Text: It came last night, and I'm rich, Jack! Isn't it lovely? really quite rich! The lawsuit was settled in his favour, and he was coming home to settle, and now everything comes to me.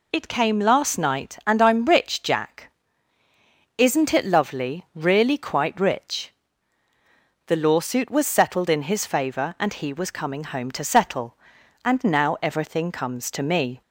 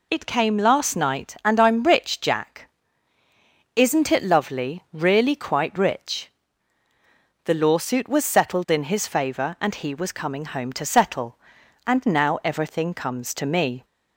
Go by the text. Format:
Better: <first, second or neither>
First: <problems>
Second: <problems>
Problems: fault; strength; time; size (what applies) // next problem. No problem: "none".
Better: neither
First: none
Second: none